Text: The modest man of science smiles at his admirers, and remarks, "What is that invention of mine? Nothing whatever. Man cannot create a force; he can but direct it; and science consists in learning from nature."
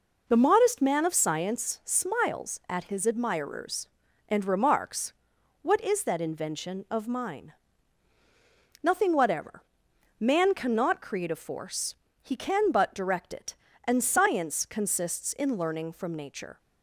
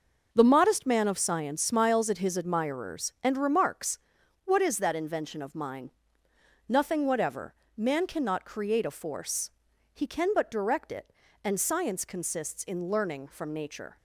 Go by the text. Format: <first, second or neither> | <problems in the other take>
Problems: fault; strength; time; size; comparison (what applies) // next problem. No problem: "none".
neither | none